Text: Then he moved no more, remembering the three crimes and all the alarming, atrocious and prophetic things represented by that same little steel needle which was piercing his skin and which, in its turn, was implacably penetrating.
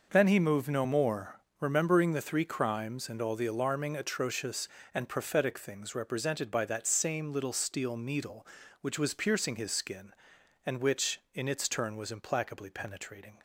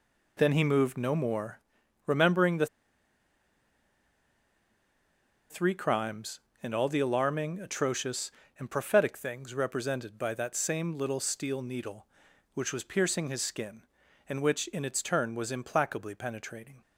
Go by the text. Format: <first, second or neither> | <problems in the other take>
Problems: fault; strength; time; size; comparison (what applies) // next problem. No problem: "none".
first | pauses between "the" and "three"; strong; at 2.6 s; 2.8 s long